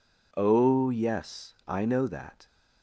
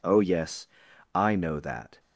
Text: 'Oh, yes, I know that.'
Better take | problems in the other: neither | none

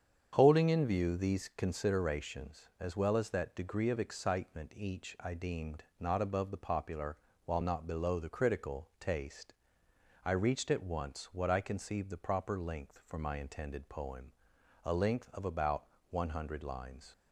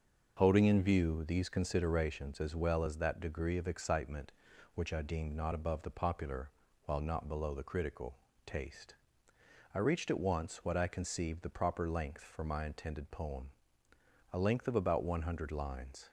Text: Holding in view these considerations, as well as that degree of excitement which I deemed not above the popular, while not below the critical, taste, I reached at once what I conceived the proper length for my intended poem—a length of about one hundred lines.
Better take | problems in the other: second | starts louder than the rest; strong; until 1.3 s; 7.5 dB; also in the second // says "each" for "which"; at 4.7 s // pauses between "deemed" and "not"; slight; at 5.8 s; 0.18 s long // pauses between "about" and "one"; slight; at 15.8 s; 0.24 s long

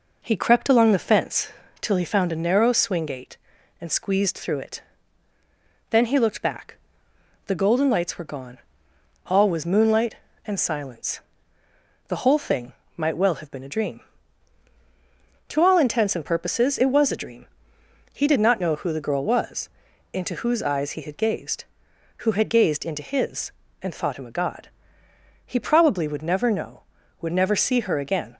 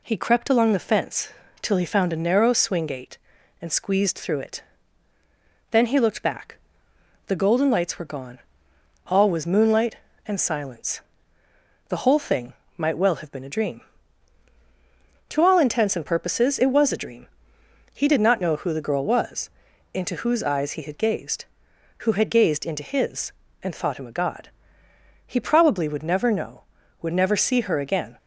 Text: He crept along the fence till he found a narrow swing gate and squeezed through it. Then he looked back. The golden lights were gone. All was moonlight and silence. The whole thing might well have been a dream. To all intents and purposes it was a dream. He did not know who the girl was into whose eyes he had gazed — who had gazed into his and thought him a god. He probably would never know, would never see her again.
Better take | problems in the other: second | starts louder than the rest; noticeable; until 1.8 s; 4.5 dB // pauses between "fence" and "till"; slight; at 1.4 s; 0.30 s long; slight in the second // pauses between "thing" and "might"; slight; at 12.7 s; 0.24 s long; slight in the second // pauses between "was" and "into"; at 19.6 s; 0.44 s long; also in the second

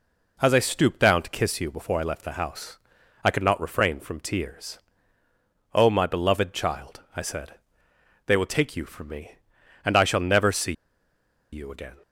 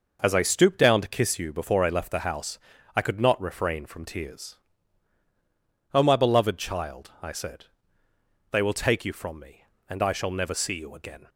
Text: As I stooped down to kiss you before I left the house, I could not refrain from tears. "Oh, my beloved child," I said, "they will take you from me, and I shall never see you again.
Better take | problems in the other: second | pauses between "see" and "you"; noticeable; at 10.7 s; 0.79 s long

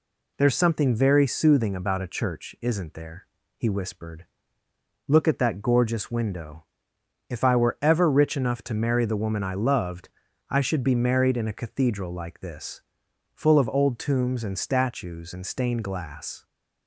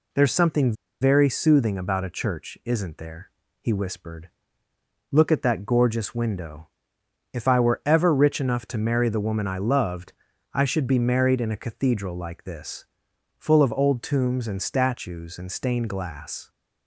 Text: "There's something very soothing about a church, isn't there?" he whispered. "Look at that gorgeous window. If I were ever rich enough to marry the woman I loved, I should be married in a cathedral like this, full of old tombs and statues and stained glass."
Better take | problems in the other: first | pauses between "something" and "very"; slight; at 0.7 s; 0.28 s long

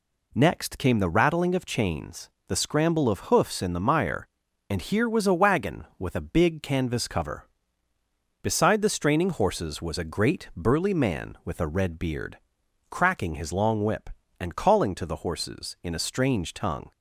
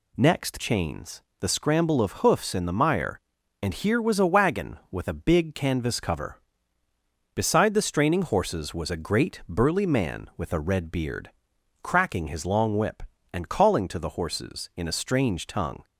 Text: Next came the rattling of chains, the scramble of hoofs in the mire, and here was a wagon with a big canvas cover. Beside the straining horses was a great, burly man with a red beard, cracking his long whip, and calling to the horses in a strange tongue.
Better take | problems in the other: first | skips "came the rattling of"; at 0.5 s

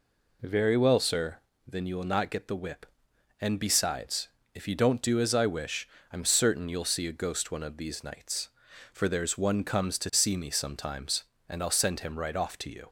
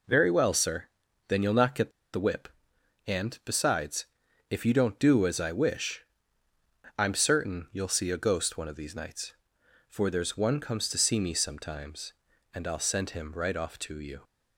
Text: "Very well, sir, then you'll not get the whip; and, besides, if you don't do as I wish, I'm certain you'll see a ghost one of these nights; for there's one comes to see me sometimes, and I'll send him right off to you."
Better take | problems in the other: first | pauses between "get" and "the"; slight; at 1.9 s; 0.23 s long

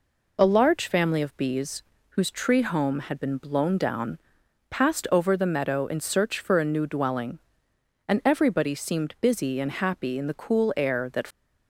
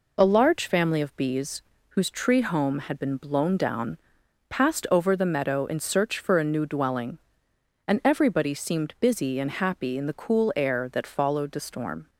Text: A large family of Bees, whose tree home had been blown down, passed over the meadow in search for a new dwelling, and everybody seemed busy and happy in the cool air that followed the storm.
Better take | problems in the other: second | stops before "followed the storm"; at 11.2 s

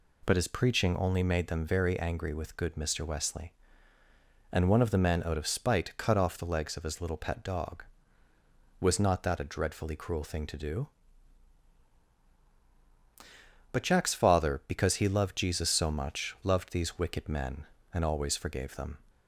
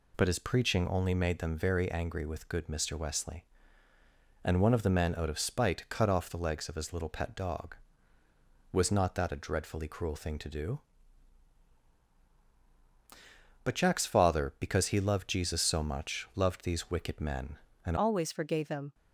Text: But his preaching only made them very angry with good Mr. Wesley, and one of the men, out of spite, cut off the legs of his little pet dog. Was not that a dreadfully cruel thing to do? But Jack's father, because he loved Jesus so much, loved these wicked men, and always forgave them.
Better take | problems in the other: first | changes voice at "always"; from 17.9 s on; 1.0 s long

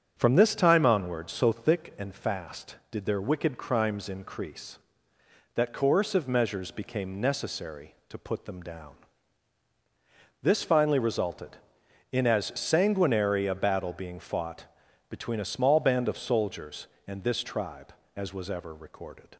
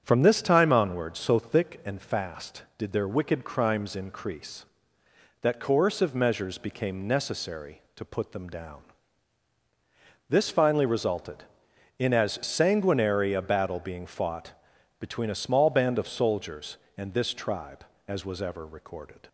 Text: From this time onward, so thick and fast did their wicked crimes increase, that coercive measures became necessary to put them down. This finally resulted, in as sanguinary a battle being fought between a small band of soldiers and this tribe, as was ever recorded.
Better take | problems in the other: neither | starts louder than the rest; strong; the same in both // pauses between "fought" and "between"; the same in both

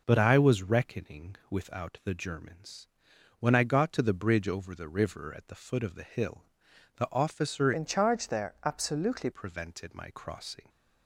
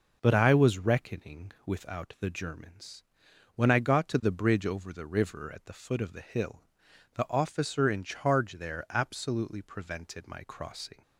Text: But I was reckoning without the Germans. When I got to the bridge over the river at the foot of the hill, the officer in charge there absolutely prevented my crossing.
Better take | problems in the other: second | changes voice from "in" to "absolutely"; from 7.7 to 9.2 s; 1.5 s long

